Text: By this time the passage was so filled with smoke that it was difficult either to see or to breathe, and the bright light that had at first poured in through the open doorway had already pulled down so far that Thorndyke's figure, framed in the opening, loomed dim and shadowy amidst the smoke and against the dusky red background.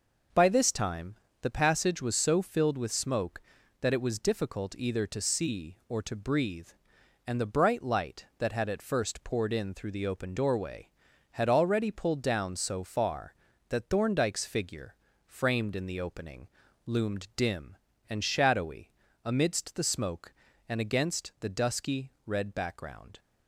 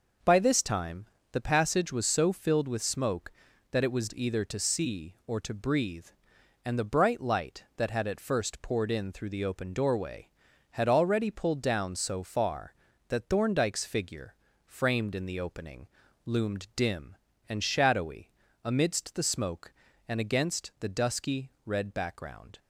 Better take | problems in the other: first | pauses between "time" and "the"; slight; at 1.0 s; 0.24 s long; slight in the first // skips "difficult"; at 4.1 s // pauses between "shadowy" and "amidst"; slight; at 18.3 s; 0.34 s long; slight in the first

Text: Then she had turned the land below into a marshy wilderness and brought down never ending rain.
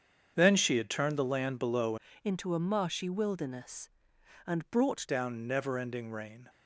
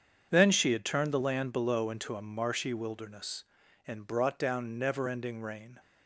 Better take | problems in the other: second | starts louder than the rest; strong; until 1.3 s; 7.5 dB; strong in the second // changes voice from "into" to "brought"; from 2.2 to 5.0 s; 2.8 s long

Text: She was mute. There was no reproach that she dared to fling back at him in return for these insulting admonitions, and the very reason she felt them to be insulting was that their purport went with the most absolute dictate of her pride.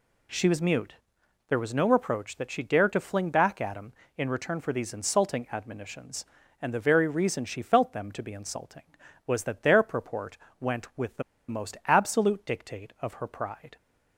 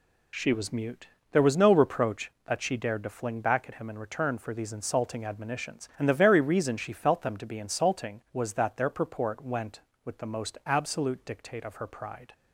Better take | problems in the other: second | pauses between "purport" and "went"; slight; at 10.3 s; 0.24 s long // pauses between "the" and "most"; slight; at 11.2 s; 0.27 s long

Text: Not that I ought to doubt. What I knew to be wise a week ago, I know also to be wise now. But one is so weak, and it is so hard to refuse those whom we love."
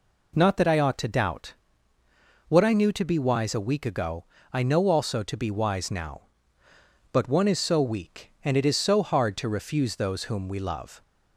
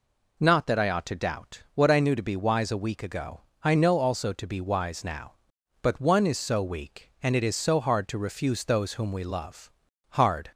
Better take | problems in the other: first | goes on to say "Hard"; slight; from 10.0 s on; 0.42 s long

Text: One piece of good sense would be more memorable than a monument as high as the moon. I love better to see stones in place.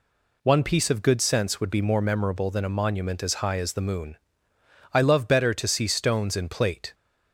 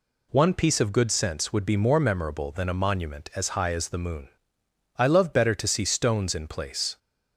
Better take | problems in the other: second | says "plate" for "place"; at 6.4 s

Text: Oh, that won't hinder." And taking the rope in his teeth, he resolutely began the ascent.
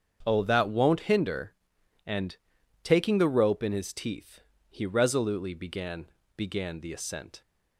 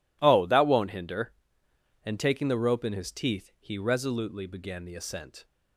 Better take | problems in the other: second | starts louder than the rest; strong; until 1.2 s; 7.5 dB // pauses between "And" and "taking"; noticeable; at 2.3 s; 0.46 s long // says "began" twice; at 6.3 s

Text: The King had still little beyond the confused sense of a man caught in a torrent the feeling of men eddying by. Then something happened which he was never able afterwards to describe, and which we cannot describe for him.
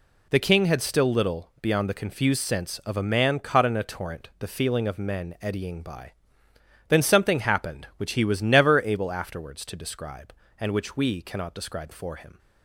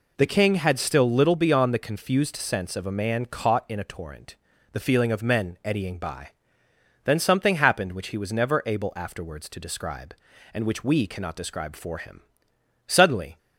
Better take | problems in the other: first | pauses between "torrent" and "the"; at 4.3 s; 0.38 s long // goes on to say "Suddenly"; from 12.8 s on; 0.50 s long

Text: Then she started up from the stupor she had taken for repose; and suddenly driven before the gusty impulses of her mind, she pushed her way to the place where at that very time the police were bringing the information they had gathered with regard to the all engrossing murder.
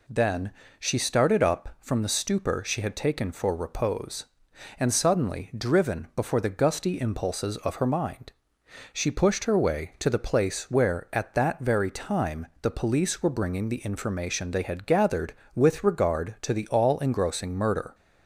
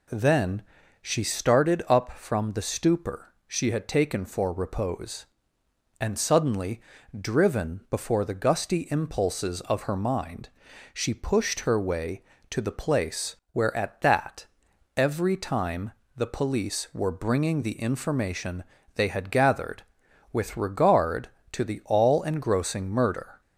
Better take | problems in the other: first | pauses between "Then" and "she"; at 0.6 s; 0.38 s long; slight in the first // pauses between "suddenly" and "driven"; at 6.8 s; 0.40 s long // pauses between "place" and "where"; slight; at 13.3 s; 0.18 s long // says "every" for "very"; at 14.9 s // pauses between "time" and "the"; slight; at 15.9 s; 0.26 s long // pauses between "information" and "they"; slight; at 18.6 s; 0.32 s long

